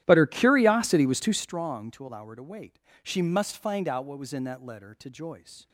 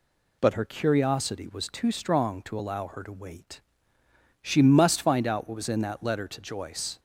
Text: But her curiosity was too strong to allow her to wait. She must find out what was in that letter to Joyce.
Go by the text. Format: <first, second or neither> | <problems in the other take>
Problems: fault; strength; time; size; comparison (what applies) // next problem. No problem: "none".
second | starts louder than the rest; strong; until 1.6 s; 12.5 dB